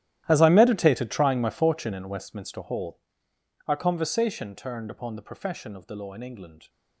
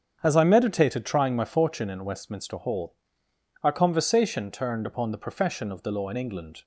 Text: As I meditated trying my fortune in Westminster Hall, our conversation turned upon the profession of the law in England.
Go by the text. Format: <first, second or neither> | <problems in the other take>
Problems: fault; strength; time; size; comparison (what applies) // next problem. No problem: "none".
second | gets quieter; strong; throughout; 17 dB // starts louder than the rest; strong; until 1.2 s; 13 dB; strong in the second